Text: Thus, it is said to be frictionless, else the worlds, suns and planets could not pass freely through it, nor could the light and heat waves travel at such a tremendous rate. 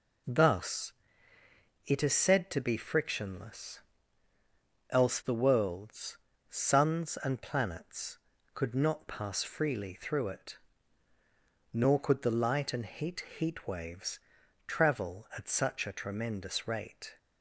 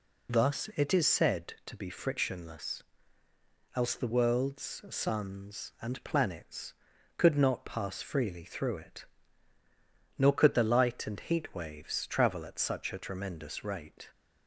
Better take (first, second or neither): second